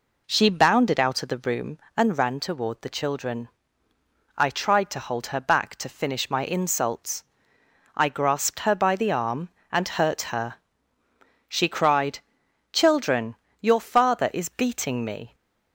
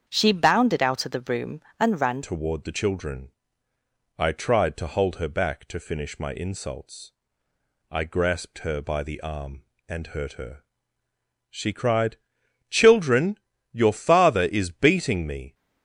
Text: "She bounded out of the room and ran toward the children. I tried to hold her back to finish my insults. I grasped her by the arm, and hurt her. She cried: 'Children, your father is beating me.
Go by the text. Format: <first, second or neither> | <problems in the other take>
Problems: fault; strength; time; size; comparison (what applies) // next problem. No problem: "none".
first | starts louder than the rest; strong; until 1.0 s; 7.5 dB // changes voice at "toward"; from 2.2 s on; 13.3 s long